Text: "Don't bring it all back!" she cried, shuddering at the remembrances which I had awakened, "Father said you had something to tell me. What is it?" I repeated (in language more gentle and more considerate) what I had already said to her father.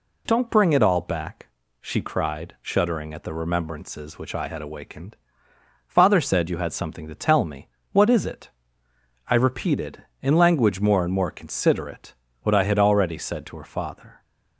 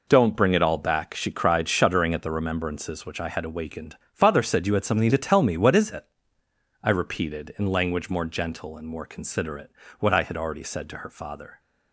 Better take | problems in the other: second | skips "gentle"; at 11.0 s

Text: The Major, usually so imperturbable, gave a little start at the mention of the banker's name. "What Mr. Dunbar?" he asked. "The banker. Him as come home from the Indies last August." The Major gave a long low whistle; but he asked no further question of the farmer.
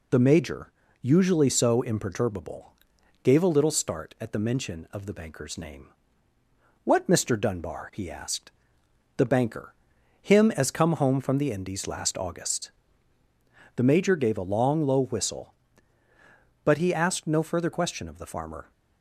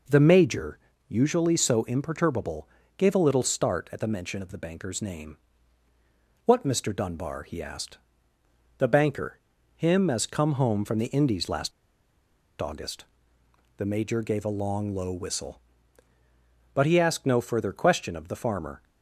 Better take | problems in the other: first | pauses between "last" and "August"; noticeable; at 11.7 s; 0.89 s long

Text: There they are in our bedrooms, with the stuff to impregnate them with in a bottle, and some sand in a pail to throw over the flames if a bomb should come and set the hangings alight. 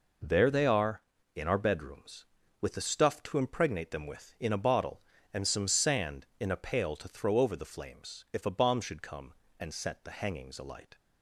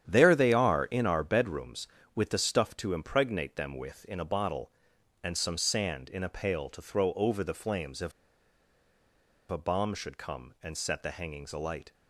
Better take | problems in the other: first | starts louder than the rest; strong; until 1.1 s; 9.5 dB // pauses between "if" and "a"; strong; at 8.1 s; 1.3 s long

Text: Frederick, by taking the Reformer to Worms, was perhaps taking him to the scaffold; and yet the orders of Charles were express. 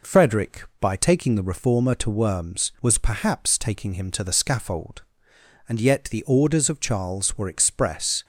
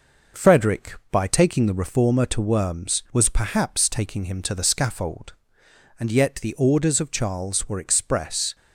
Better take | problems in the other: first | gets quieter; throughout; 4 dB

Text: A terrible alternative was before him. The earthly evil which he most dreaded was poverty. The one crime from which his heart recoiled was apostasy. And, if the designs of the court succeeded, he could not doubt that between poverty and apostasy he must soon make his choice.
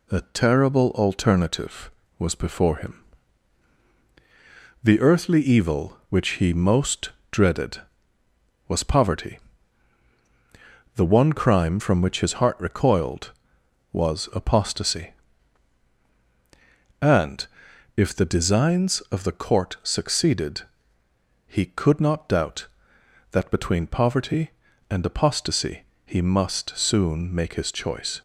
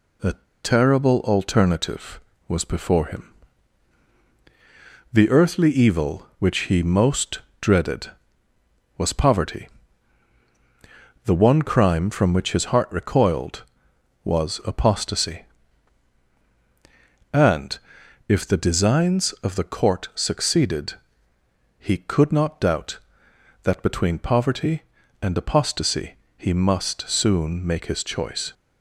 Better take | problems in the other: first | pauses between "A" and "terrible"; slight; at 0.3 s; 0.29 s long // pauses between "most" and "dreaded"; slight; at 7.3 s; 0.20 s long; slight in the first // pauses between "apostasy" and "he"; slight; at 26.1 s; 0.24 s long; slight in the first

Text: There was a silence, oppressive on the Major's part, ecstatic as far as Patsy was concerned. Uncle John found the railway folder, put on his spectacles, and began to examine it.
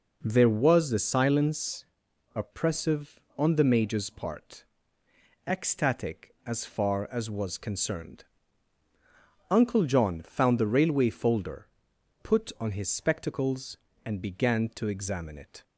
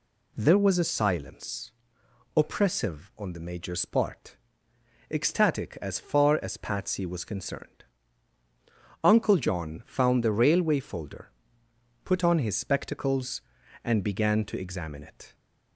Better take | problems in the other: second | skips "Patsy"; at 7.2 s

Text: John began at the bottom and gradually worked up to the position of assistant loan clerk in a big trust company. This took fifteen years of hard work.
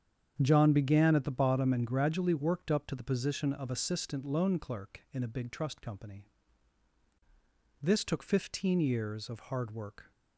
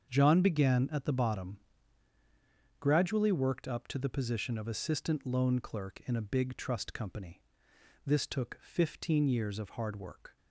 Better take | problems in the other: first | starts louder than the rest; until 1.1 s; 7 dB; strong in the first // skips "and"; at 2.1 s

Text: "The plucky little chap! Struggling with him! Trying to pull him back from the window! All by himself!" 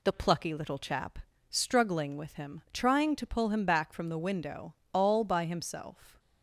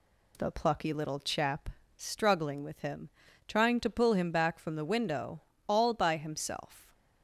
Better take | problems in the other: neither | none

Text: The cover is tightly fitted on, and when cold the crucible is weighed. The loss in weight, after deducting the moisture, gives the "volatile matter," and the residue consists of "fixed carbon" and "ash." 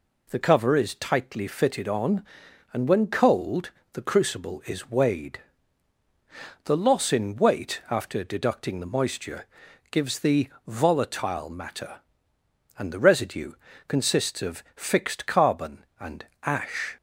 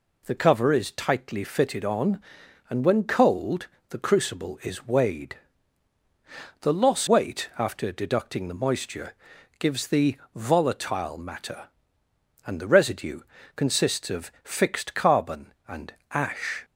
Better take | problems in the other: first | pauses between "cold" and "the"; slight; at 3.6 s; 0.22 s long; slight in the first // skips "in"; at 7.0 s // pauses between "the" and "volatile"; slight; at 10.1 s; 0.18 s long; slight in the first // pauses between "residue" and "consists"; slight; at 13.2 s; 0.34 s long; slight in the first // pauses between "and" and "ash"; slight; at 15.9 s; 0.18 s long; slight in the first

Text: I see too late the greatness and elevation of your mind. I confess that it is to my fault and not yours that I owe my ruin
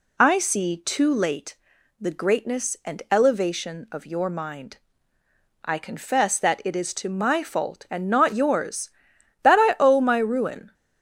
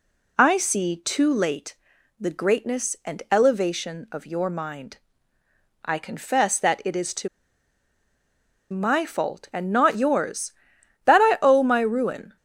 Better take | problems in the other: first | pauses between "late" and "the"; at 1.7 s; 0.44 s long; also in the first // pauses between "to" and "my"; strong; at 7.2 s; 1.4 s long

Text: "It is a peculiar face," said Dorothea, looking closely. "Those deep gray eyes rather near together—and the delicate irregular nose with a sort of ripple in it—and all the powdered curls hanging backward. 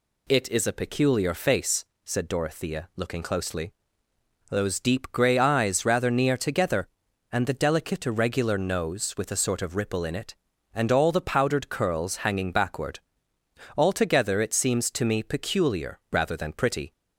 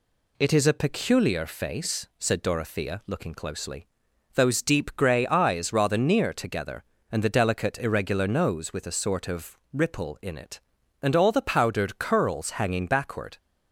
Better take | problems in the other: second | goes on to say "Altogether it seems to me peculiar rather than pretty"; strong; from 13.7 s on; 3.1 s long

